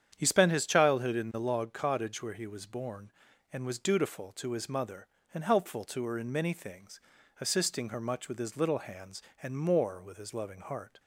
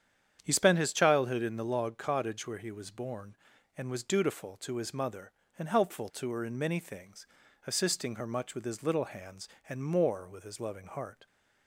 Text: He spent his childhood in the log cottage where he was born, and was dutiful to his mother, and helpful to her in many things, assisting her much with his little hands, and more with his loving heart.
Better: neither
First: starts louder than the rest; strong; until 1.1 s; 8.5 dB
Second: starts louder than the rest; strong; until 1.4 s; 8.5 dB

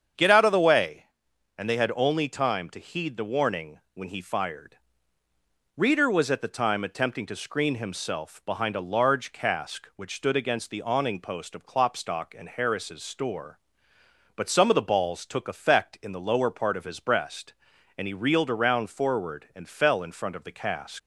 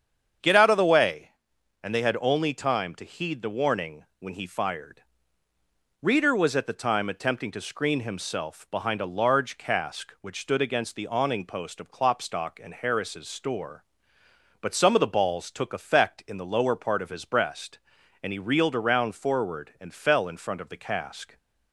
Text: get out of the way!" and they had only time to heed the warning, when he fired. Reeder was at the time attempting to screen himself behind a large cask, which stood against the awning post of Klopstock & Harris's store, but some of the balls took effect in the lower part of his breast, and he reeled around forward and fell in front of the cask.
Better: second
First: starts louder than the rest; strong; until 1.6 s; 7.5 dB // leaves "cask" unfinished; at 20.9 s; 120 ms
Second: starts louder than the rest; strong; until 1.9 s; 7.5 dB

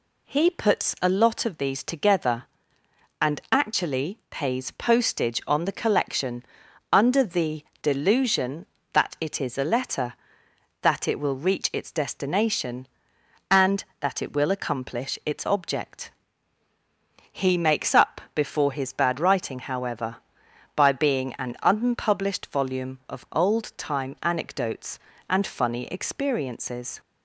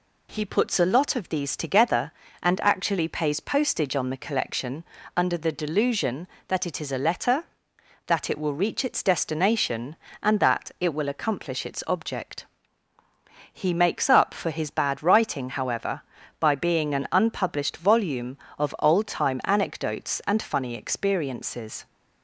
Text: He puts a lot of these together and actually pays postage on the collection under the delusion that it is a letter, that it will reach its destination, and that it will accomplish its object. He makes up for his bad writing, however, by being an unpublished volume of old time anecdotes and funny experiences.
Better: second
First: pauses between "collection" and "under"; noticeable; at 6.4 s; 0.50 s long // pauses between "the" and "delusion"; slight; at 7.6 s; 0.18 s long // says "before" for "for"; at 18.3 s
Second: pauses between "collection" and "under"; slight; at 4.8 s; 0.32 s long

